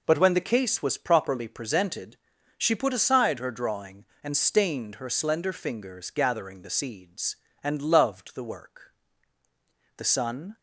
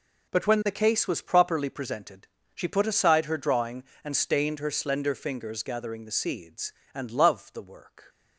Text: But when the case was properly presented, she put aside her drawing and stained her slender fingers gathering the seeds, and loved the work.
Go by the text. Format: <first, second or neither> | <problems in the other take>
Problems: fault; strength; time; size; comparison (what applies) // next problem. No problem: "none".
second | goes on to say "The sun"; from 9.9 s on; 0.60 s long